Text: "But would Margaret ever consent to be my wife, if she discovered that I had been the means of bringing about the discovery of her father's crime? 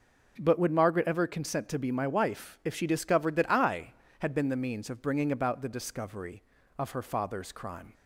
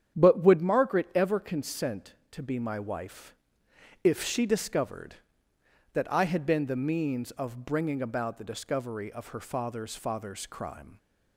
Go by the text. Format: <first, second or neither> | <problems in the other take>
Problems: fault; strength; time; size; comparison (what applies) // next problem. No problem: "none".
first | starts louder than the rest; strong; until 1.2 s; 9 dB // says "father's" twice; at 9.9 s